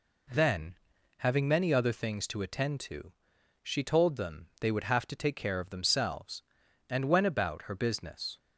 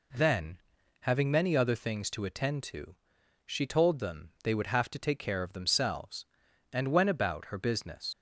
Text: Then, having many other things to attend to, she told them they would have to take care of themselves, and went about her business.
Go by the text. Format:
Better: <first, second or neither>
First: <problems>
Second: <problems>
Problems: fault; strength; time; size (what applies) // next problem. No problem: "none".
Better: first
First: none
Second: leaves "business" unfinished; at 8.1 s; 85 ms